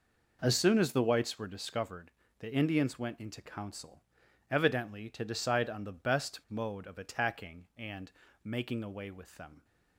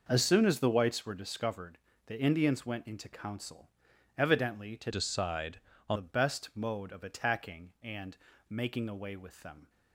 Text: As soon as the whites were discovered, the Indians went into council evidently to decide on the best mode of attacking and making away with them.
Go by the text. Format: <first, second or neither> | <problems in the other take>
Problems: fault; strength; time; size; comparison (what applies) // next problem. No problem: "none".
first | pauses between "council" and "evidently"; noticeable; at 3.6 s; 0.48 s long; noticeable in the first // changes voice from "decide" to "on"; from 4.8 to 5.9 s; 1.1 s long // pauses between "and" and "making"; slight; at 8.1 s; 0.32 s long; slight in the first